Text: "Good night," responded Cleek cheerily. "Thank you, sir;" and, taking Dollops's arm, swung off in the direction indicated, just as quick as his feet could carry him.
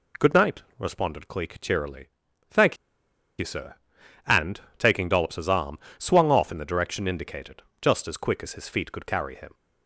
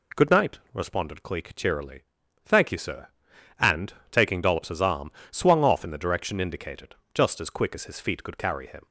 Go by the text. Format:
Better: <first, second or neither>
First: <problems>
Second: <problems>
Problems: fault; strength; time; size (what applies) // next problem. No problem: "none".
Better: second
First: pauses between "Thank" and "you"; noticeable; at 2.7 s; 0.63 s long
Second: none